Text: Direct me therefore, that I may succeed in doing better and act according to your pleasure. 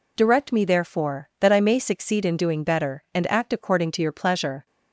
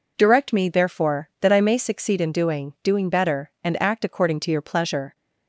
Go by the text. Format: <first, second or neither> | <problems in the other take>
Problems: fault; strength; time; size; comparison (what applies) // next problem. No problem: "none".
first | says "doing" twice; at 2.8 s